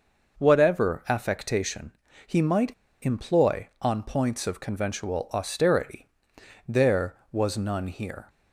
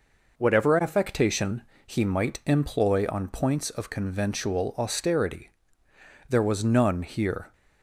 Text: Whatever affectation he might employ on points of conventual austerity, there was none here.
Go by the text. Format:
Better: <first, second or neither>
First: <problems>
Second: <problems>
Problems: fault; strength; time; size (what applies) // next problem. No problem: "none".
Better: second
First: pauses between "affectation" and "he"; slight; at 1.9 s; 0.34 s long // pauses between "might" and "employ"; slight; at 2.7 s; 0.30 s long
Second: pauses between "affectation" and "he"; slight; at 1.6 s; 0.24 s long